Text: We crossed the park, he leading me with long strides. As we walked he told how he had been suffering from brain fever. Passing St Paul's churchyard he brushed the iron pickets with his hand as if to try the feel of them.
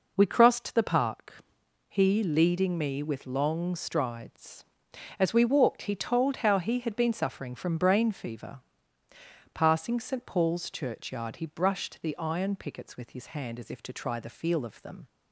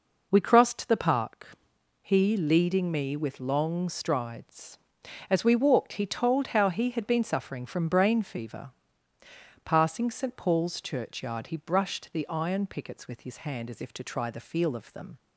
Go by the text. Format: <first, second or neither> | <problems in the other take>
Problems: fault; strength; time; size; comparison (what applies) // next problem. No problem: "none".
neither | none